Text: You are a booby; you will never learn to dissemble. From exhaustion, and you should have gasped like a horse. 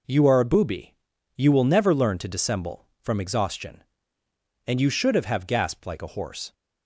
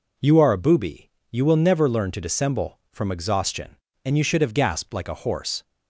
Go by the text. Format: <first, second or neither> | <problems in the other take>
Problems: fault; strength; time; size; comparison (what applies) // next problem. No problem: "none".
second | says "have" twice; at 5.2 s